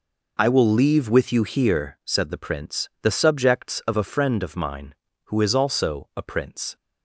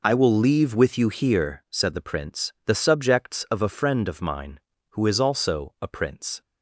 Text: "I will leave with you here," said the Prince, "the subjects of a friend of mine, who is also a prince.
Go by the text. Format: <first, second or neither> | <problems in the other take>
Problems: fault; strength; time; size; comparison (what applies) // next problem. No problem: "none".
neither | none